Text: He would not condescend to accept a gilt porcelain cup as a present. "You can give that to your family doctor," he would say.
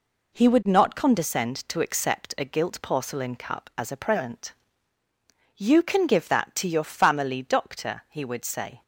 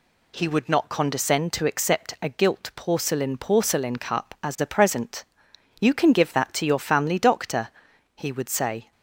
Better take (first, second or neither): first